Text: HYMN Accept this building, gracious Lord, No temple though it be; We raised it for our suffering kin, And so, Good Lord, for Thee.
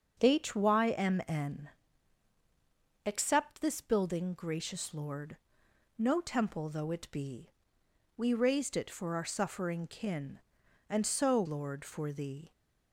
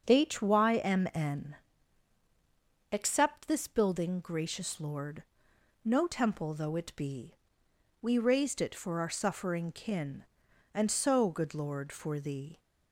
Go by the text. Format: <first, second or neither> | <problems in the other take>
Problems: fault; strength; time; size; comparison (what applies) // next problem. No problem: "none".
second | starts louder than the rest; until 1.2 s; 6.5 dB; also in the second // pauses between "HYMN" and "Accept"; strong; at 1.6 s; 1.3 s long; strong in the second // skips "Good"; at 11.4 s